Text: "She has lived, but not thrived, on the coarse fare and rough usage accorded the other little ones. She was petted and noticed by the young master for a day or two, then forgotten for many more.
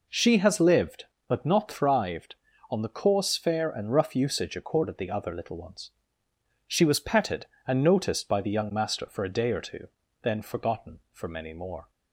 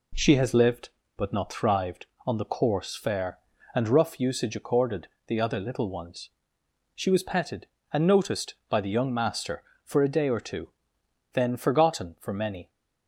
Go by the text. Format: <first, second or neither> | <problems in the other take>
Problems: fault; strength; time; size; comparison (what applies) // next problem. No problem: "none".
first | pauses between "accorded" and "the"; slight; at 5.0 s; 0.20 s long // stops before "more"; at 12.6 s